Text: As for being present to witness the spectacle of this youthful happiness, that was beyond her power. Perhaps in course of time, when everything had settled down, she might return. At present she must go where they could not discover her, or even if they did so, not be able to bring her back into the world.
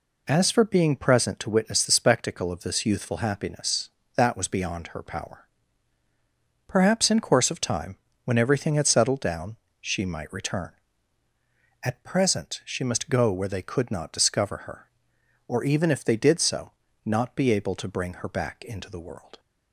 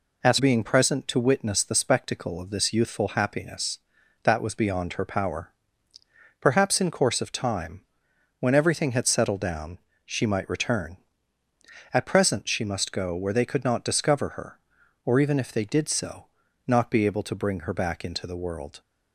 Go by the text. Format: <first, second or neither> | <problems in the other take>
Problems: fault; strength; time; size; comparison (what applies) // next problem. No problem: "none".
first | skips "for"; at 0.3 s